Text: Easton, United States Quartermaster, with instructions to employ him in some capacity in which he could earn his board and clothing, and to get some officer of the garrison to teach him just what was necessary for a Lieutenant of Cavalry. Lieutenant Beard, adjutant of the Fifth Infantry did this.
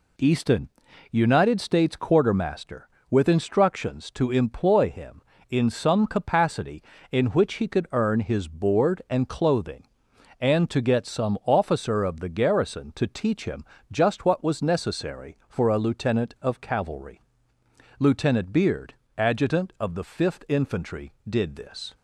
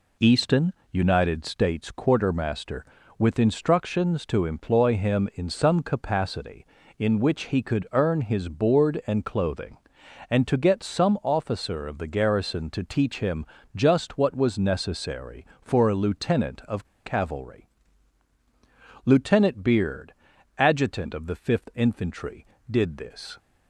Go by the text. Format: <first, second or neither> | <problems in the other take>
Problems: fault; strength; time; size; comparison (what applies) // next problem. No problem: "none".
first | pauses between "him" and "just"; slight; at 13.4 s; 0.30 s long; slight in the first // pauses between "of" and "Cavalry"; slight; at 16.8 s; 0.18 s long